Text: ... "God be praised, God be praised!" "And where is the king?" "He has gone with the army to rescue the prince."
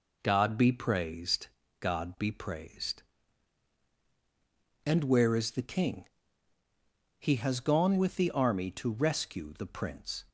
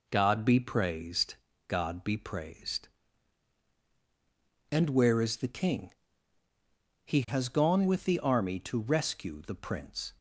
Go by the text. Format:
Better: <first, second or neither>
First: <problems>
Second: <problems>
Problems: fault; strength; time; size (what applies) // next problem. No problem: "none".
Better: neither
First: none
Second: none